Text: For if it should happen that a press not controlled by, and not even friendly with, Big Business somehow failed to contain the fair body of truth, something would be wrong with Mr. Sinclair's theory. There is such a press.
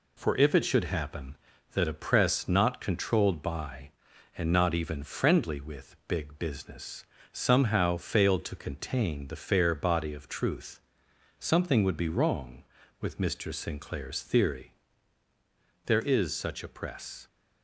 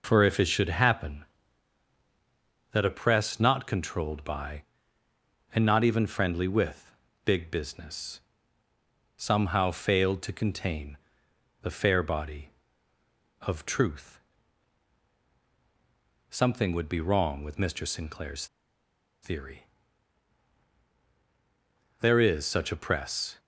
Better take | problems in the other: first | pauses between "Business" and "somehow"; noticeable; at 8.1 s; 0.98 s long; slight in the first // pauses between "contain" and "the"; noticeable; at 10.9 s; 0.66 s long // pauses between "Sinclair's" and "theory"; noticeable; at 18.4 s; 0.77 s long

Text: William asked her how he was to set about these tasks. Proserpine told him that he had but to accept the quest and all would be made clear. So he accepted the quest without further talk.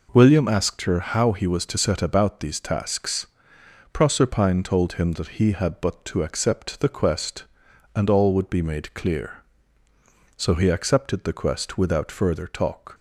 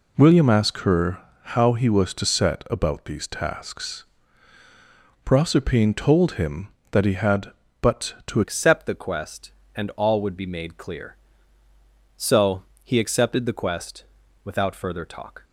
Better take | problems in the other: first | pauses between "her" and "how"; slight; at 1.1 s; 0.24 s long // changes voice at "accept"; from 8.4 s on; 7.0 s long // pauses between "So" and "he"; slight; at 12.6 s; 0.22 s long // pauses between "quest" and "without"; at 14.0 s; 0.40 s long

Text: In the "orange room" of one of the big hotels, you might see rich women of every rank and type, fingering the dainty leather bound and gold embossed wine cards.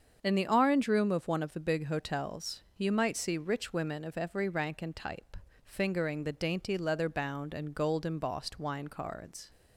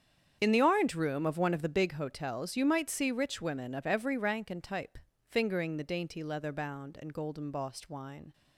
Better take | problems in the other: first | starts louder than the rest; strong; until 1.4 s; 8 dB; also in the first // stops before "cards"; at 8.3 s

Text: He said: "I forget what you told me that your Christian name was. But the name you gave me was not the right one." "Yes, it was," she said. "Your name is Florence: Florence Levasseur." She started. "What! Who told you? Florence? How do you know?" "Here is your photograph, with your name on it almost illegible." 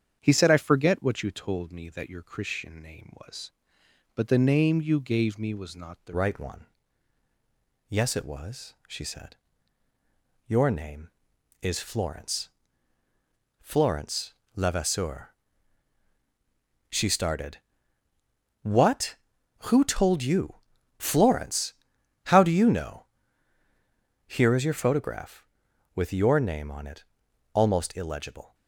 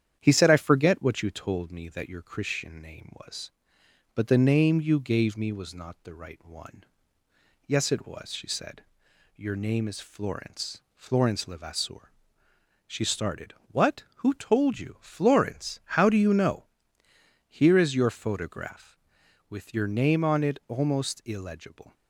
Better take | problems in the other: second | starts louder than the rest; strong; until 1.2 s; 8 dB; strong in the second // changes voice at "right"; from 6.1 s on; 22.4 s long // pauses between "Florence" and "Levasseur"; slight; at 14.3 s; 0.20 s long // pauses between "it" and "almost"; noticeable; at 27.0 s; 0.48 s long

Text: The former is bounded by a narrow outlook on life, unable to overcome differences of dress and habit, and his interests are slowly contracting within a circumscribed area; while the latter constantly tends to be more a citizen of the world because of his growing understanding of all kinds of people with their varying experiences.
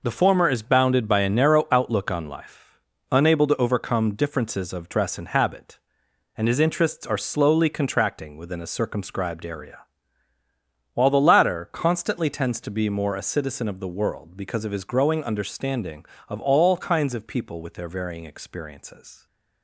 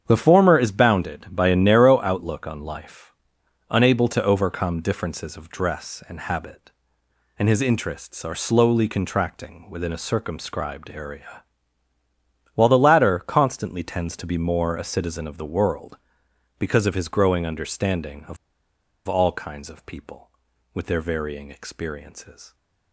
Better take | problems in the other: first | starts louder than the rest; strong; until 1.0 s; 8 dB // pauses between "of" and "all"; noticeable; at 18.3 s; 0.71 s long

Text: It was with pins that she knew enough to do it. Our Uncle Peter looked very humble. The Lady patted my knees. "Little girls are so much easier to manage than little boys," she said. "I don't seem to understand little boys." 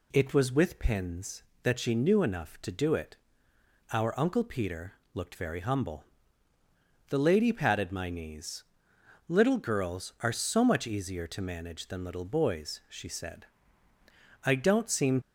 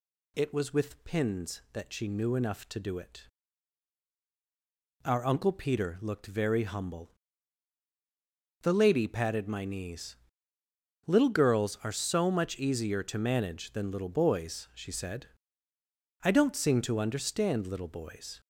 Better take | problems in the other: second | pauses between "Peter" and "looked"; slight; at 4.9 s; 0.20 s long // stops before "to understand little boys"; at 15.2 s

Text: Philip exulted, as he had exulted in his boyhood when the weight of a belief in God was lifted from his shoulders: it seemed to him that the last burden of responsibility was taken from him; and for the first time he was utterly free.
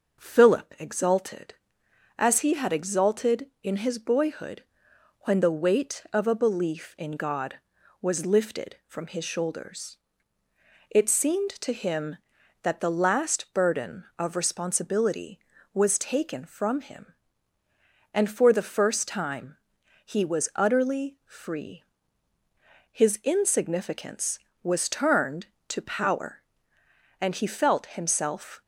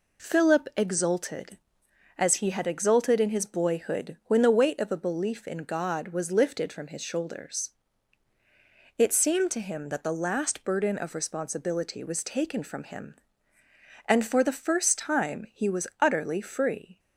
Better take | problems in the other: second | pauses between "boyhood" and "when"; noticeable; at 4.6 s; 0.58 s long // pauses between "time" and "he"; noticeable; at 19.5 s; 0.50 s long // goes on to say "His insignificance was turned to power and he felt himself"; strong; from 22.9 s on; 5.7 s long

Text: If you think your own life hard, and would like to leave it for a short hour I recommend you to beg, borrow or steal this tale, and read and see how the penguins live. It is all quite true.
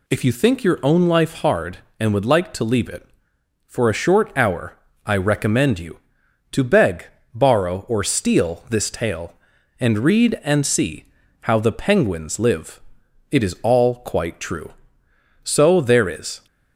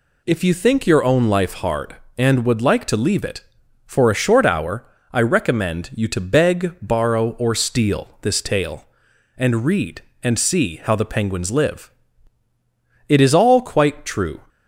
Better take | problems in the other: second | pauses between "hour" and "I"; slight; at 4.7 s; 0.30 s long; slight in the second // pauses between "see" and "how"; slight; at 11.0 s; 0.36 s long // goes on to say "So there is"; noticeable; from 15.4 s on; 1.0 s long

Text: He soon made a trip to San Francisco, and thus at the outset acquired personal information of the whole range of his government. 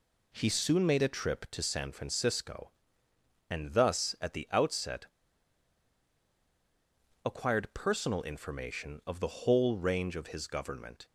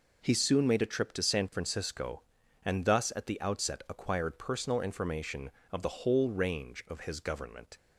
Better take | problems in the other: second | pauses between "outset" and "acquired"; strong; at 5.0 s; 2.1 s long

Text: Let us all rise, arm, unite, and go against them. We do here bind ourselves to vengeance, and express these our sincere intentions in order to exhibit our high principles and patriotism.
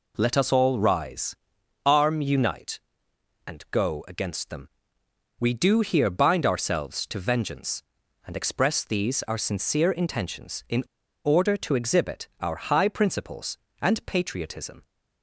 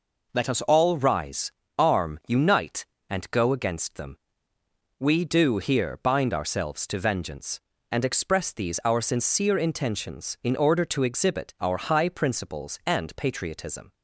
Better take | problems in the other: second | pauses between "in" and "order"; at 10.8 s; 0.41 s long

